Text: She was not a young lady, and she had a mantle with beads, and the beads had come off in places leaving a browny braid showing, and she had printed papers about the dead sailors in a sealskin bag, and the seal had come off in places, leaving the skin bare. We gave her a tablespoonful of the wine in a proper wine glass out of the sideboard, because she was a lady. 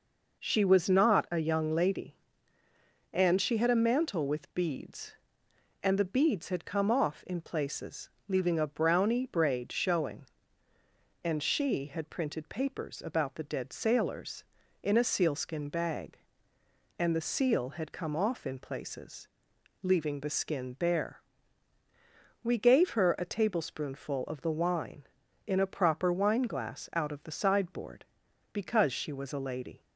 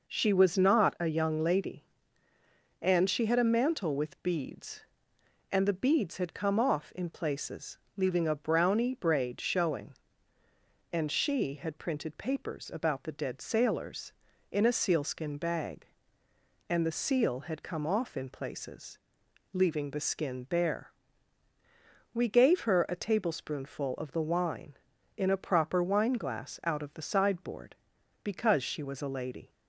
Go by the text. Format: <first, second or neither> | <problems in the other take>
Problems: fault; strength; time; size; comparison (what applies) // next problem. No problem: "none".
neither | pauses between "places" and "leaving"; slight; the same in both